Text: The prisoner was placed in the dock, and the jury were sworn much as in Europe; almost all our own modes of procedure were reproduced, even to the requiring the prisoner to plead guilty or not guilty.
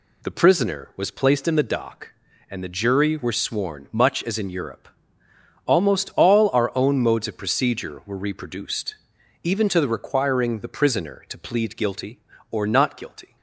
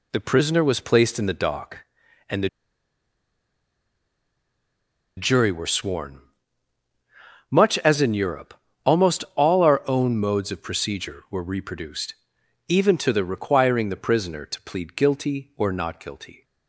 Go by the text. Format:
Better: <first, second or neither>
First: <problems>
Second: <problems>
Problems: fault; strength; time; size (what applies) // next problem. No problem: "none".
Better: first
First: none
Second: pauses between "the" and "jury"; strong; at 2.4 s; 2.6 s long // pauses between "sworn" and "much"; strong; at 6.1 s; 1.3 s long